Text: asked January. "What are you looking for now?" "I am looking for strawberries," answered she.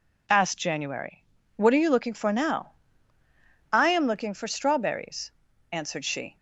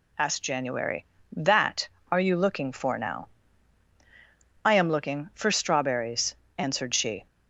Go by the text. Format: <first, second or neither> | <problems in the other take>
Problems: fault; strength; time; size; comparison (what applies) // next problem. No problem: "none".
first | says "That" for "What"; at 1.3 s